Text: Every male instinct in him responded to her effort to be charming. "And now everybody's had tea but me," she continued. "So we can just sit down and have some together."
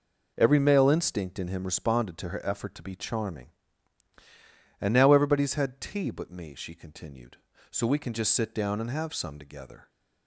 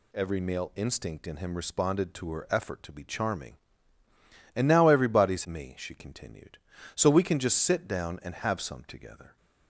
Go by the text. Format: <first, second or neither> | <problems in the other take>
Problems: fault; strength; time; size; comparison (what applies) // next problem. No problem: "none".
first | skips "had tea but"; at 5.4 s